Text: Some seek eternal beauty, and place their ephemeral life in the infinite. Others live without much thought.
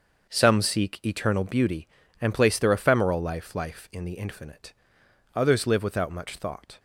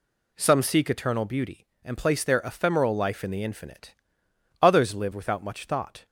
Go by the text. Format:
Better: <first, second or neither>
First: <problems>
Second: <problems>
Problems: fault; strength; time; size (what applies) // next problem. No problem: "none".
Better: second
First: starts louder than the rest; until 1.3 s; 6.5 dB // says "life" twice; at 3.5 s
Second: none